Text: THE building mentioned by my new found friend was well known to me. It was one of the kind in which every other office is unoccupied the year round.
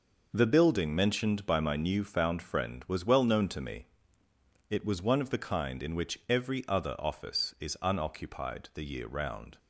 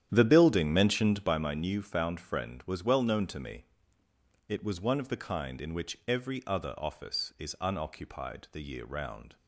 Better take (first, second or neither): first